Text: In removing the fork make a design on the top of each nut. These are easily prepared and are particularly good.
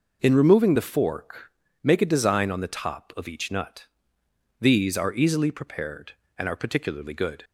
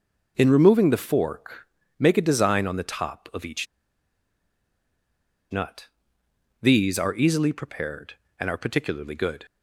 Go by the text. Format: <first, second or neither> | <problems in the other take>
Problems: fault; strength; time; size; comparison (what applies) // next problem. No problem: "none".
first | pauses between "fork" and "make"; slight; at 1.6 s; 0.30 s long; slight in the first // pauses between "each" and "nut"; strong; at 3.6 s; 1.8 s long